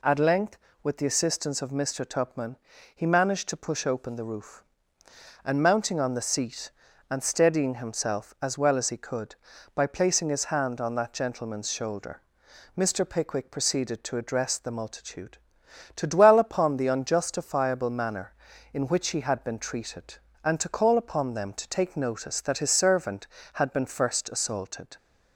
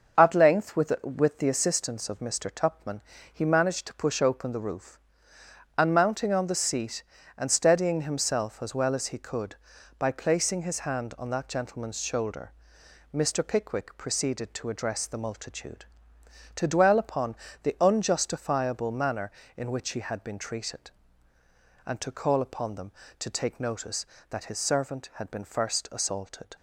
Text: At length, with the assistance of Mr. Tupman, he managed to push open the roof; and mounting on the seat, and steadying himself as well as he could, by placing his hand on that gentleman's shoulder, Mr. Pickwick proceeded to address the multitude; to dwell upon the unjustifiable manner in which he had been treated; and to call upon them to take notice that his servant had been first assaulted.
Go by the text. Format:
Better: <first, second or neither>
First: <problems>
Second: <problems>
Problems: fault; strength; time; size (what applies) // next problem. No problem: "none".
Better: first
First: none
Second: starts louder than the rest; until 1.2 s; 6.5 dB // says "with" twice; at 1.0 s // pauses between "upon" and "the"; slight; at 17.3 s; 0.28 s long